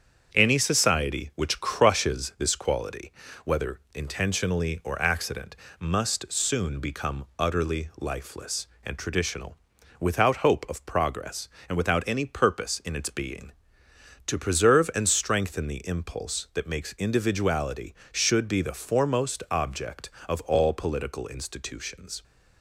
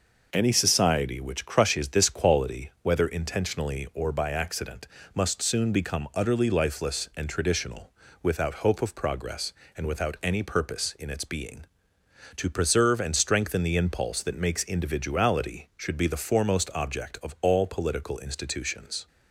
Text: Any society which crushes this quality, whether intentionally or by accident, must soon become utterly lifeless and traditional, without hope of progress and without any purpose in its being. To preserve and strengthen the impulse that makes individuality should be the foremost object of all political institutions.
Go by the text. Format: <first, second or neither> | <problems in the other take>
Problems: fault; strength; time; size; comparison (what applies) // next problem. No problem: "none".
second | starts louder than the rest; strong; until 1.3 s; 7.5 dB // skips "by"; at 5.0 s